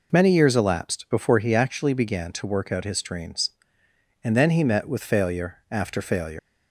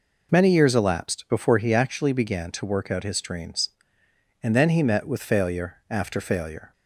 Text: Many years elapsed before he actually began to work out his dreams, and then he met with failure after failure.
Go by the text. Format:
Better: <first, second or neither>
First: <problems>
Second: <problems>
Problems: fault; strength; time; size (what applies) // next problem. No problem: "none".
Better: second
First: leaves "failure" unfinished; at 6.3 s; 135 ms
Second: none